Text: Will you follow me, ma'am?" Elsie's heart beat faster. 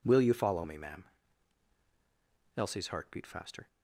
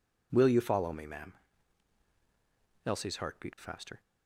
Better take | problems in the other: neither | none

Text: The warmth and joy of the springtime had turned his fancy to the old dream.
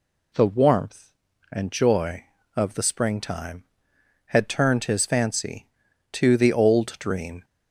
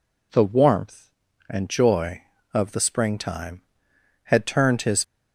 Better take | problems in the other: first | stops before "fancy to the old dream"; at 5.0 s

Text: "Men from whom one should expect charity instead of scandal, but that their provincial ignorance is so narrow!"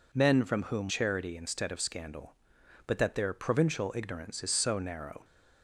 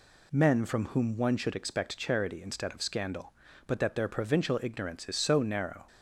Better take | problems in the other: second | skips "one should expect"; at 0.8 s

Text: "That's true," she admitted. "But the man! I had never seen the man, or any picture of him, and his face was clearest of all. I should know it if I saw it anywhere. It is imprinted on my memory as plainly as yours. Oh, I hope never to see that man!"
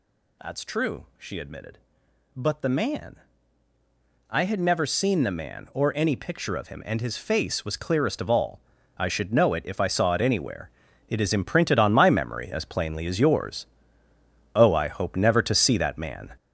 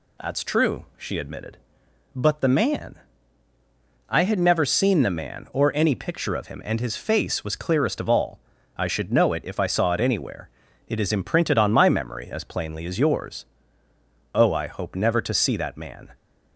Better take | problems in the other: second | gets louder; strong; throughout; 7 dB

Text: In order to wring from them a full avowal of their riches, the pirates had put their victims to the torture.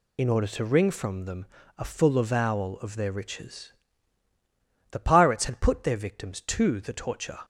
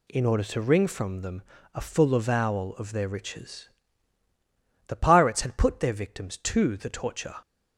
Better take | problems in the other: second | loses the start of "In"; at 0.1 s; 70 ms // pauses between "them" and "a"; slight; at 1.4 s; 0.32 s long; slight in the second

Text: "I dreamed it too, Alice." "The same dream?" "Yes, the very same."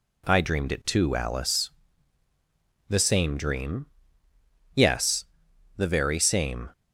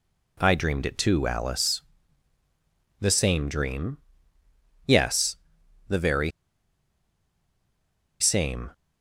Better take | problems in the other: first | pauses between "very" and "same"; strong; at 6.3 s; 1.8 s long

